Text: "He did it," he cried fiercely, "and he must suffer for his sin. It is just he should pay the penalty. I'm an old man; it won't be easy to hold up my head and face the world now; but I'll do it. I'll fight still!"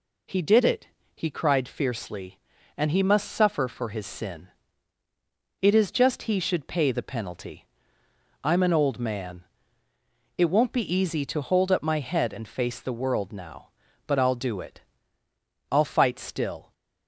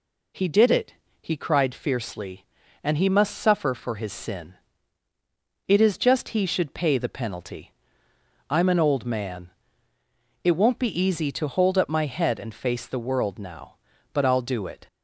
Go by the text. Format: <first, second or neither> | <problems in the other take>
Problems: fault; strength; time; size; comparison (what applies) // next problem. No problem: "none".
first | stops before "I'll fight still"; at 14.8 s